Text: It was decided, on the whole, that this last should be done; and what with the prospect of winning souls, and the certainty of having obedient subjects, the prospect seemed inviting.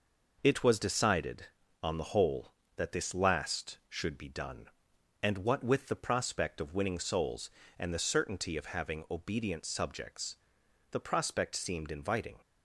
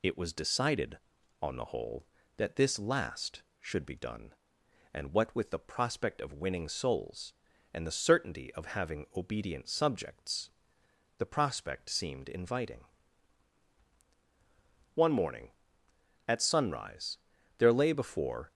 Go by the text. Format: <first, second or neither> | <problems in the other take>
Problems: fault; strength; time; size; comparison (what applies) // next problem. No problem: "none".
first | goes on to say "One morning at sunrise there lay before"; strong; from 14.9 s on; 3.5 s long